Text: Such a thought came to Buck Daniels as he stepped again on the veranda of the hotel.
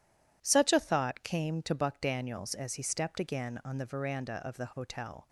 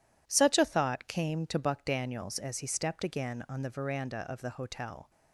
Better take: neither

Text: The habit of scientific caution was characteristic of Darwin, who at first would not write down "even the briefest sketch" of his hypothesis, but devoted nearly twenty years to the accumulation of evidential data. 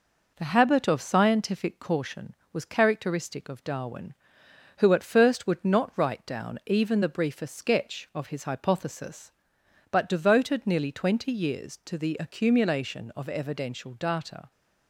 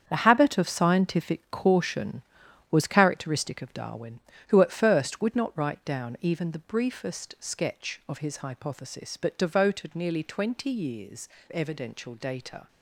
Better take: first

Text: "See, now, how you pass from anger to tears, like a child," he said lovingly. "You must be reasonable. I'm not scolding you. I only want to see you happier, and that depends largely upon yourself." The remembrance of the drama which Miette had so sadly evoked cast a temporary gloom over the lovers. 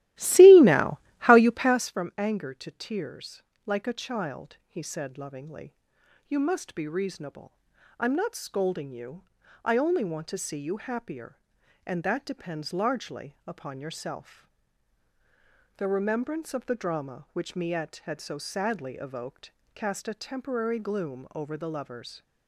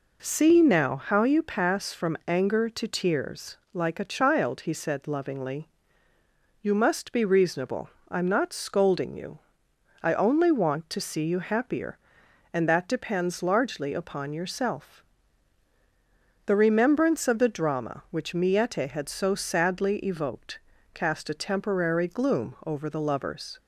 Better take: second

